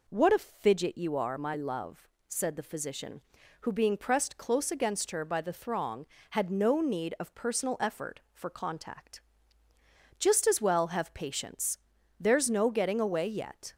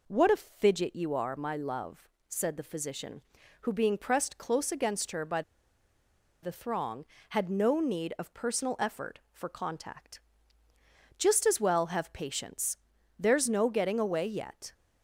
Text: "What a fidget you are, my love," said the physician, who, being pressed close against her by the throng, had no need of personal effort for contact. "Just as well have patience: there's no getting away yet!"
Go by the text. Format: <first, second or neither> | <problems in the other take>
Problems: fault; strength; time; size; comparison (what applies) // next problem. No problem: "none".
first | pauses between "by" and "the"; at 5.4 s; 1.0 s long